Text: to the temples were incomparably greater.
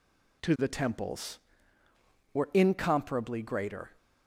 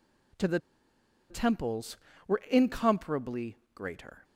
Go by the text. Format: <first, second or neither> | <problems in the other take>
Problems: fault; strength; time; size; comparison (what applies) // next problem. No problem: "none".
first | pauses between "the" and "temples"; noticeable; at 0.5 s; 0.71 s long // pauses between "incomparably" and "greater"; slight; at 3.5 s; 0.16 s long